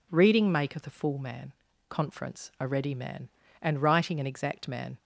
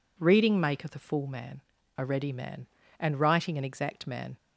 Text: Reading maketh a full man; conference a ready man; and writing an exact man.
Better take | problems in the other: first | skips "conference"; at 1.7 s

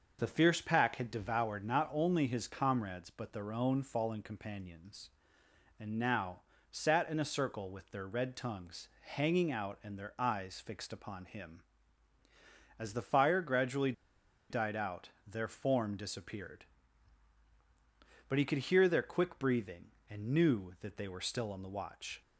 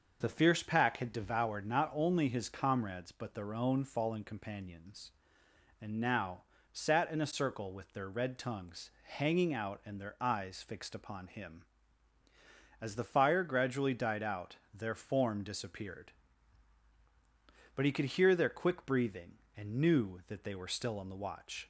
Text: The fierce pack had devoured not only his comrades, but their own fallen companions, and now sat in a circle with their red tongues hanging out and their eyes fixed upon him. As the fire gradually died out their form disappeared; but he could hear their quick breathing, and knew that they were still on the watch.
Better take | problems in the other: second | starts louder than the rest; until 1.2 s; 6 dB; also in the second // pauses between "now" and "sat"; slight; at 6.4 s; 0.28 s long; slight in the second // pauses between "gradually" and "died"; noticeable; at 13.9 s; 0.58 s long

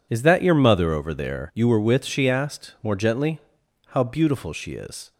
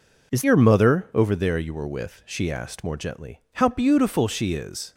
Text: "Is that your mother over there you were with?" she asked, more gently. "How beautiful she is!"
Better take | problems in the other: first | skips "that"; at 0.4 s

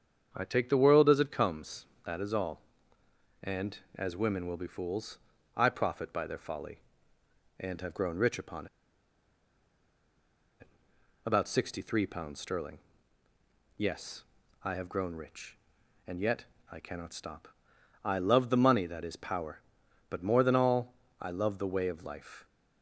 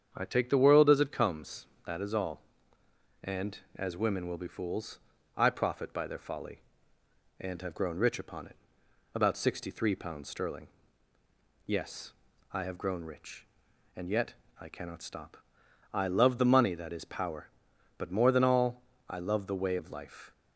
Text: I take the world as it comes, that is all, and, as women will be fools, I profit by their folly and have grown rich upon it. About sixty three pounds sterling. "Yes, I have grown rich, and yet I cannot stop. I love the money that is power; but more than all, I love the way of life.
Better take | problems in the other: second | starts louder than the rest; strong; until 1.3 s; 7.5 dB; strong in the second // pauses between "upon" and "it"; strong; at 8.6 s; 1.9 s long // pauses between "yet" and "I"; slight; at 16.4 s; 0.26 s long; slight in the second

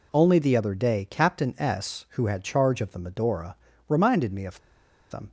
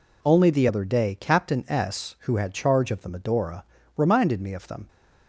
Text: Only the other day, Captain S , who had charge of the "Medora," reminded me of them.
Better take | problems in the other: second | pauses between "of" and "them"; noticeable; at 4.5 s; 0.53 s long

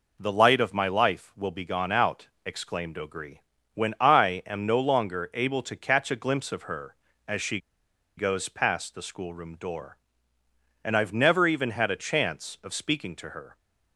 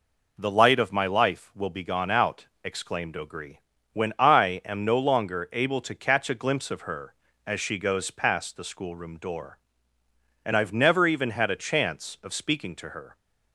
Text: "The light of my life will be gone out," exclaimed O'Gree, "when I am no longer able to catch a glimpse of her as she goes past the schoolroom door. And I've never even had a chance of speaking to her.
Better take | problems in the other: second | pauses between "she" and "goes"; noticeable; at 7.5 s; 0.59 s long

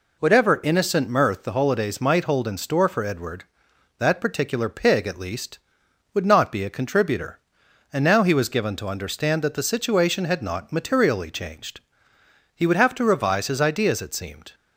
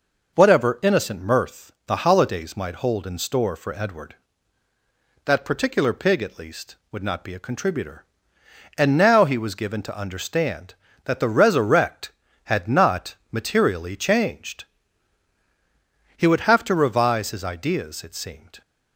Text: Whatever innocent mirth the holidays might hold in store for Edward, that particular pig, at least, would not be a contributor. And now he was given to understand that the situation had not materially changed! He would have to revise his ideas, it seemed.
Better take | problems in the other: first | says "resurrect" for "situation"; at 11.2 s // pauses between "not" and "materially"; slight; at 13.1 s; 0.18 s long

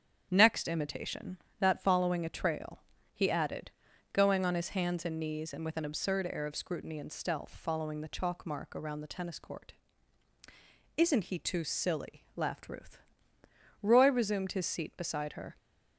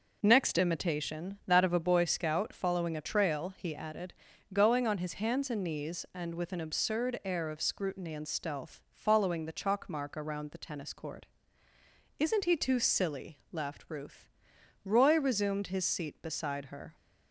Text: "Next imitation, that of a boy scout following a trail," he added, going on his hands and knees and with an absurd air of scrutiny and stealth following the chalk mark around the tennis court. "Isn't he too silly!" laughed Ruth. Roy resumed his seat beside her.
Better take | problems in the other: second | starts louder than the rest; strong; until 1.3 s; 8 dB // skips "of a boy scout"; at 1.8 s

